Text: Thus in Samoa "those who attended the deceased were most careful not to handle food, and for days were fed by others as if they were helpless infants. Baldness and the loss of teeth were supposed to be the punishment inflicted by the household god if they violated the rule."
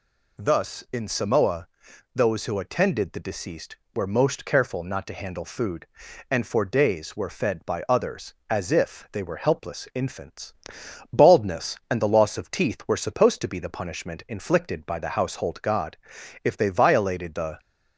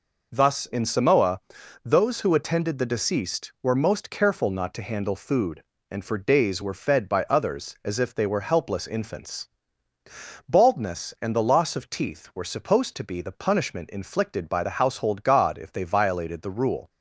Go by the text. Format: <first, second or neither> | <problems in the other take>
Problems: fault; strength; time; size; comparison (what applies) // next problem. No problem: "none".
second | pauses between "Samoa" and "those"; noticeable; at 1.6 s; 0.48 s long; also in the second // pauses between "god" and "if"; noticeable; at 15.9 s; 0.48 s long // stops before "rule"; at 17.5 s